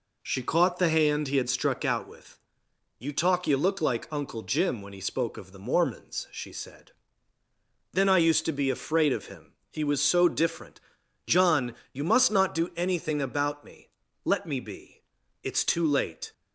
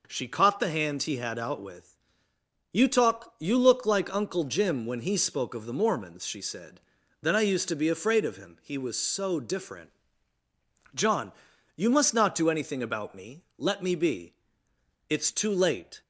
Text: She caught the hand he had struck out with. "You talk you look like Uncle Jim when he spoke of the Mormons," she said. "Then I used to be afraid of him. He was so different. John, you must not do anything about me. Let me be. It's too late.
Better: first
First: none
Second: skips "struck"; at 1.3 s

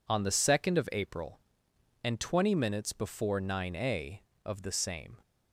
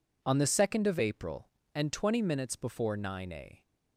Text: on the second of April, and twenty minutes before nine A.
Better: second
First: goes on to say "of the same"; noticeable; from 4.4 s on; 0.72 s long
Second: none

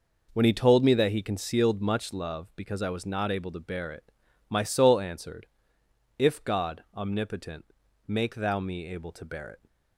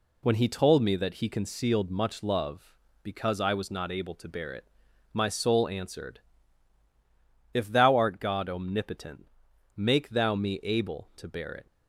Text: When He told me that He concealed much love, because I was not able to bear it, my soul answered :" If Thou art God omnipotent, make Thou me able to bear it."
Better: second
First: skips "Thou art"; at 6.4 s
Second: none

